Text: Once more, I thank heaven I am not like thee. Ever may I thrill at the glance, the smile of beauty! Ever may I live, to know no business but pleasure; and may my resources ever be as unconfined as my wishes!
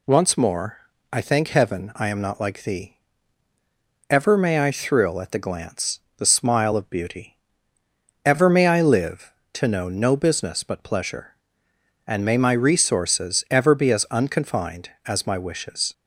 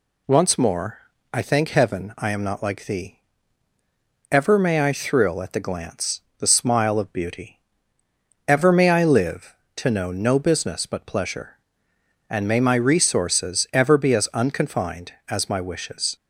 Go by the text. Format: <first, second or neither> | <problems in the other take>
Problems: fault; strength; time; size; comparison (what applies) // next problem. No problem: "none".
neither | none